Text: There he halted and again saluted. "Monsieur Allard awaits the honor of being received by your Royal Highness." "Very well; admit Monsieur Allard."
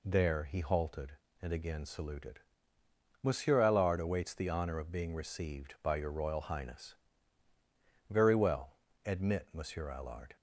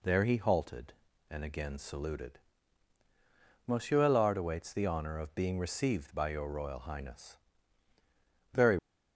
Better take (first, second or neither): first